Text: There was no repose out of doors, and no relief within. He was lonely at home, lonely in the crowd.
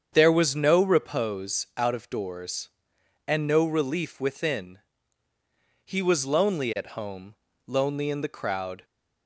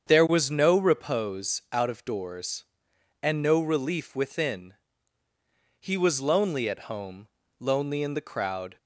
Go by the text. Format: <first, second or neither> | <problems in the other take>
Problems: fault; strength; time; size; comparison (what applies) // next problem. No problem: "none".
neither | starts louder than the rest; strong; the same in both